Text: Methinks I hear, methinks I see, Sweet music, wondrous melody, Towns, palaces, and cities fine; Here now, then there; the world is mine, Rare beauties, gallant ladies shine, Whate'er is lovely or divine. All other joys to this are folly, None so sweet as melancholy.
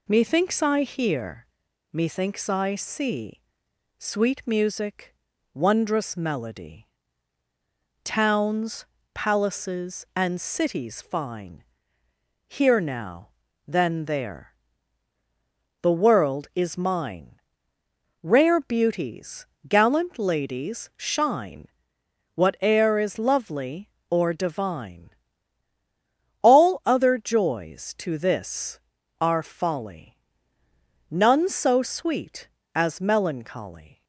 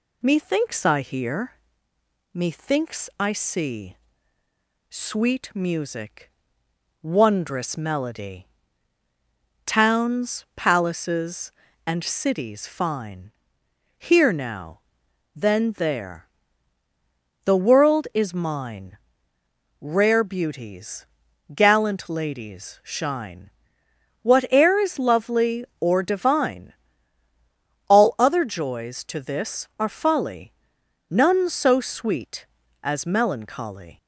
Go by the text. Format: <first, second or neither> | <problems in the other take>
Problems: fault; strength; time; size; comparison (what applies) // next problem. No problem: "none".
neither | none